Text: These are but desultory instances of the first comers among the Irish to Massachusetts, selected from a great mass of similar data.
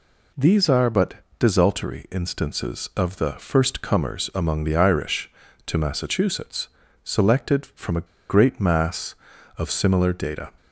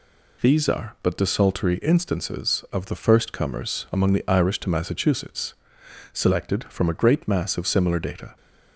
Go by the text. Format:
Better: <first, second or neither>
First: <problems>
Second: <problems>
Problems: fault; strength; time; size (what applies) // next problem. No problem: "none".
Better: second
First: pauses between "but" and "desultory"; slight; at 1.1 s; 0.26 s long // pauses between "a" and "great"; slight; at 8.0 s; 0.23 s long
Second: none